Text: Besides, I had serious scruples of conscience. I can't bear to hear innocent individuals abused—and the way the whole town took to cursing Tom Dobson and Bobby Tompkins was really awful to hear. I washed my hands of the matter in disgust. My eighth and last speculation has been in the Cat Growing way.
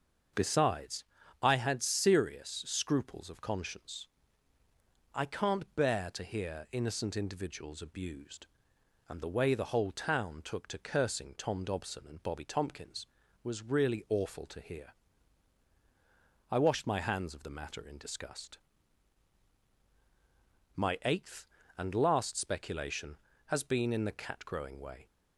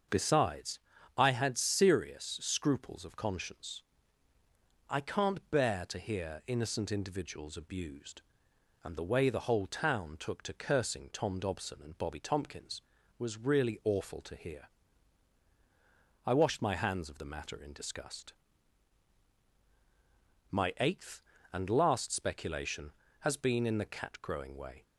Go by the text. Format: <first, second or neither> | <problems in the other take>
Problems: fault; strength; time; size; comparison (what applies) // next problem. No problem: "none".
neither | starts louder than the rest; the same in both